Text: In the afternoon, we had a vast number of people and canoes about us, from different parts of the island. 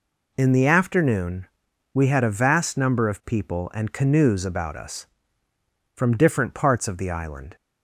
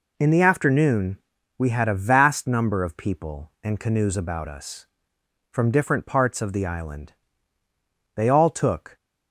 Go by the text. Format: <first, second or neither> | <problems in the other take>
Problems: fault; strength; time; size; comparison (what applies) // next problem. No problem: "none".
first | goes on to say "They all took"; noticeable; from 8.1 s on; 0.82 s long